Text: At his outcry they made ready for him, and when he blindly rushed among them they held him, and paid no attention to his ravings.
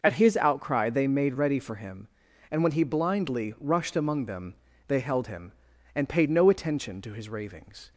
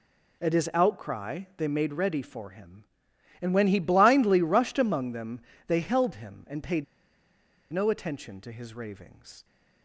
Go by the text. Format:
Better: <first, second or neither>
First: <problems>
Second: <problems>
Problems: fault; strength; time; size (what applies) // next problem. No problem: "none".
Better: first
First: pauses between "them" and "they"; slight; at 4.5 s; 0.32 s long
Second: pauses between "them" and "they"; slight; at 5.4 s; 0.26 s long // pauses between "paid" and "no"; noticeable; at 6.8 s; 0.87 s long